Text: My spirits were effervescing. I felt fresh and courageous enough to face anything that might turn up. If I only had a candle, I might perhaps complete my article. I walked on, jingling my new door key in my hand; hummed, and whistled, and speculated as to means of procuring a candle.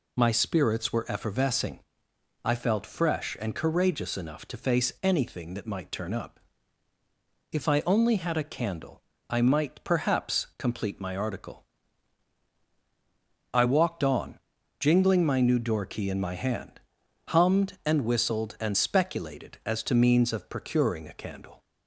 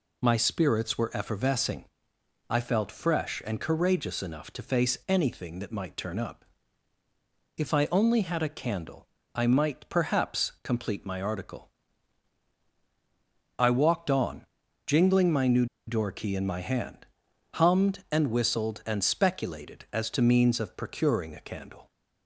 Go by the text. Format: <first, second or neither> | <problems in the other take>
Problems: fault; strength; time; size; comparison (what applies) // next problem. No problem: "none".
first | pauses between "new" and "door"; slight; at 15.6 s; 0.22 s long